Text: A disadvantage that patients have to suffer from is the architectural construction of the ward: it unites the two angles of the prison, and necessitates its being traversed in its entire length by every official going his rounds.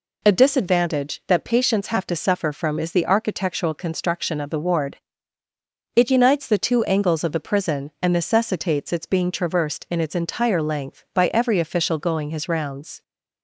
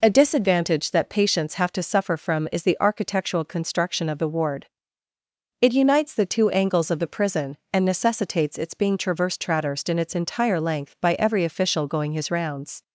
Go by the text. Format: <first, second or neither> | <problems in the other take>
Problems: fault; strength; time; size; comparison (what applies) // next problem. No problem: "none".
first | says "traversed" twice; at 9.4 s